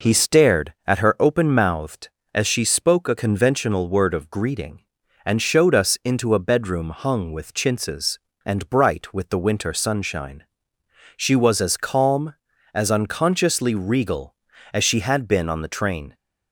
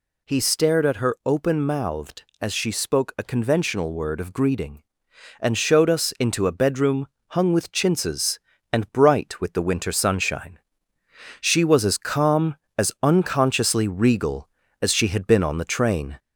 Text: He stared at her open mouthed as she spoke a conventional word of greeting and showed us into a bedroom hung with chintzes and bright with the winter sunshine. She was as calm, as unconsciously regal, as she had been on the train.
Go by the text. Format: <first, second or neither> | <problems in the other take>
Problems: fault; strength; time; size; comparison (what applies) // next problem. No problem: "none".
first | gets louder; slight; throughout; 2 dB // pauses between "bedroom" and "hung"; slight; at 7.0 s; 0.22 s long